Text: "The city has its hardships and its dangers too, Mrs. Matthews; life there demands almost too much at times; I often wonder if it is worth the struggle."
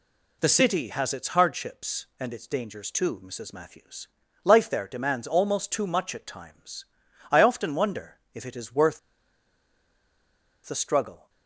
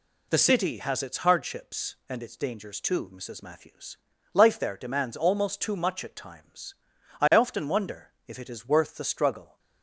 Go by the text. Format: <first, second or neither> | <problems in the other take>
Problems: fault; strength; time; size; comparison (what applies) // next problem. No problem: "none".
second | pauses between "worth" and "the"; strong; at 8.9 s; 1.6 s long